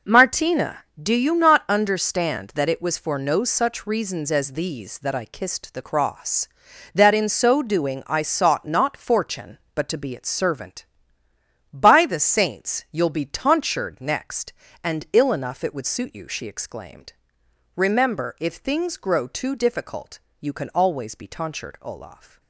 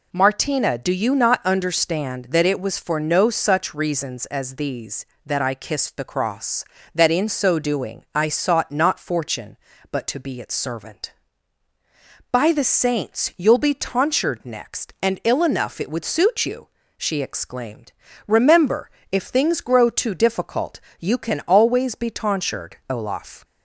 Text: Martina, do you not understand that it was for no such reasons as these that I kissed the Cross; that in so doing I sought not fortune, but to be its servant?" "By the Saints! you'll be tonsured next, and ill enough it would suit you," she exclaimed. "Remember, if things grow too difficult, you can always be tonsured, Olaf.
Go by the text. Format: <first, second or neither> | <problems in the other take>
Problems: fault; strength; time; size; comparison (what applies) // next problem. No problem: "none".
neither | none